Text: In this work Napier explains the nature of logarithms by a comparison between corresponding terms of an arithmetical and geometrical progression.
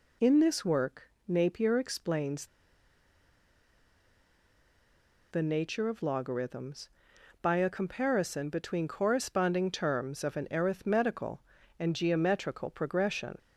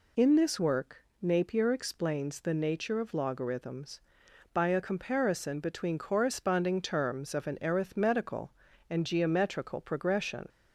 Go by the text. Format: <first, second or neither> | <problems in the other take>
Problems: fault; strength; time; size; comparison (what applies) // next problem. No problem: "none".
second | pauses between "work" and "Napier"; slight; at 1.0 s; 0.18 s long; slight in the second // pauses between "explains" and "the"; strong; at 2.4 s; 2.8 s long